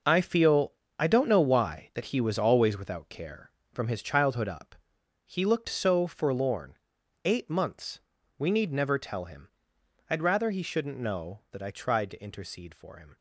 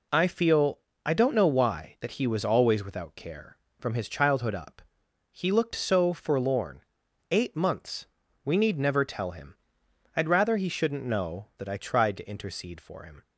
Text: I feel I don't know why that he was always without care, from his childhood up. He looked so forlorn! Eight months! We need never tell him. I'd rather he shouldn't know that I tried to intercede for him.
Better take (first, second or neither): second